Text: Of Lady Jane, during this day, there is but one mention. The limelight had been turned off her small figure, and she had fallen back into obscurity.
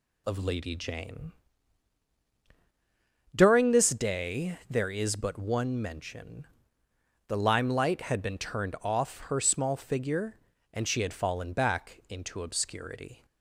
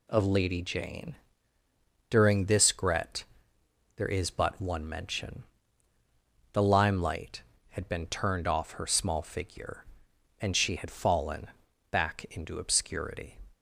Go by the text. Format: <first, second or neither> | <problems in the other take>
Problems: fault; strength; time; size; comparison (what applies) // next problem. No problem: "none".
first | says "gret" for "day"; at 2.7 s // pauses between "fallen" and "back"; at 11.4 s; 0.44 s long